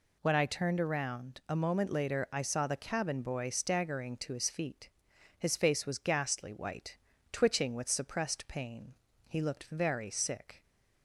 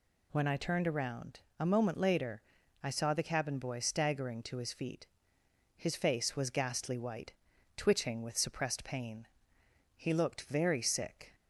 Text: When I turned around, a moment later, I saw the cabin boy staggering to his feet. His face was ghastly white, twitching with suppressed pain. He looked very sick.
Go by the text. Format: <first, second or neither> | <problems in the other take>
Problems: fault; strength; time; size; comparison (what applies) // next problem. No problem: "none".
neither | none